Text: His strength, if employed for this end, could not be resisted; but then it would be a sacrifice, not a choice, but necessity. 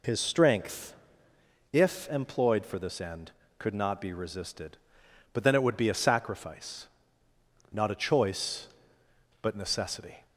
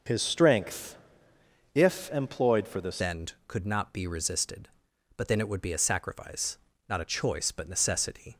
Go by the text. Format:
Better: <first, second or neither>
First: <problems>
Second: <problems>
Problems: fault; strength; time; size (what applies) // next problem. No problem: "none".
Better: first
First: none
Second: starts louder than the rest; until 1.8 s; 6.5 dB // changes voice at "end"; from 3.0 s on; 5.3 s long